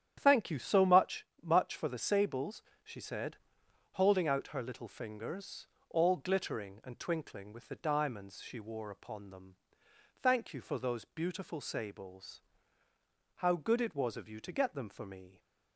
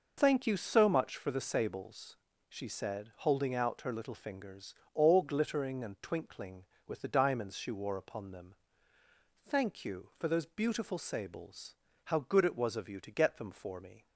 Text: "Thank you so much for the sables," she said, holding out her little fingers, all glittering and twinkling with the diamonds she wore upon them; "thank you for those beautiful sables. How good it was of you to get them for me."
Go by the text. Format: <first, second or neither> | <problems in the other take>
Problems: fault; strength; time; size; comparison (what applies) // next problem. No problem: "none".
second | starts louder than the rest; strong; until 1.1 s; 10 dB // says "much" twice; at 1.4 s